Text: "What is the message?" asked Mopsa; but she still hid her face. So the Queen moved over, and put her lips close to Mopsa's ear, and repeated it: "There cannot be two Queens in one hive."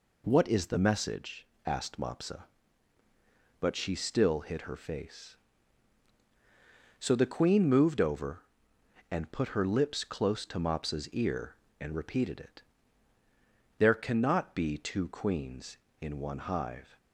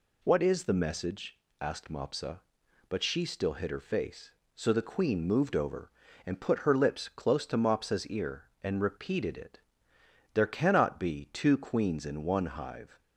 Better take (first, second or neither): neither